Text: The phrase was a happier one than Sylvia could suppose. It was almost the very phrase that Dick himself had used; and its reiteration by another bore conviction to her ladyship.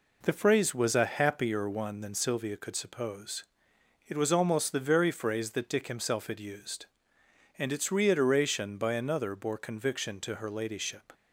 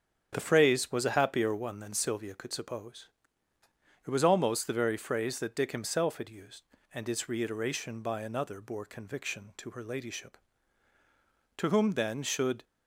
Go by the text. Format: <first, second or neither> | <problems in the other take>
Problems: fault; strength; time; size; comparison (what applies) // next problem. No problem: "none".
first | starts louder than the rest; strong; until 1.3 s; 7.5 dB // goes on to say "To whom then should"; noticeable; from 11.5 s on; 1.0 s long